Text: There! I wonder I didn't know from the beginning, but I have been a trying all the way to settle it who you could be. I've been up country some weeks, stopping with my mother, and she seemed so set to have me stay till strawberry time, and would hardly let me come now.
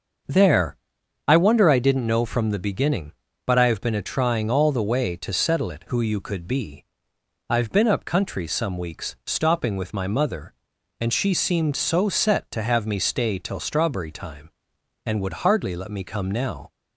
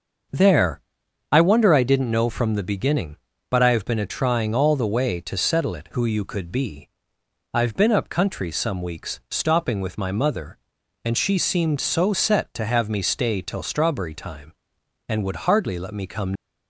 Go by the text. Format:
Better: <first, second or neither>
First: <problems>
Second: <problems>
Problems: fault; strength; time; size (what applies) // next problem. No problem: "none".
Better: first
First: starts louder than the rest; until 1.7 s; 6.5 dB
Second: starts louder than the rest; until 1.8 s; 6.5 dB // stops before "now"; at 16.3 s